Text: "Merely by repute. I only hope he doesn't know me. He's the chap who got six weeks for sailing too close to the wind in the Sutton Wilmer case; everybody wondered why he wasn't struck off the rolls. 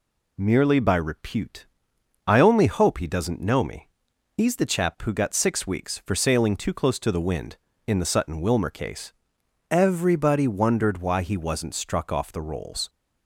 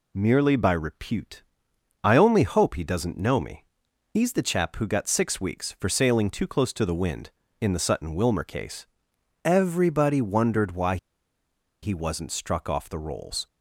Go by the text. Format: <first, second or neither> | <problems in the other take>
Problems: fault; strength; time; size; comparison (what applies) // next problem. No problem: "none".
first | pauses between "why" and "he"; noticeable; at 10.9 s; 0.85 s long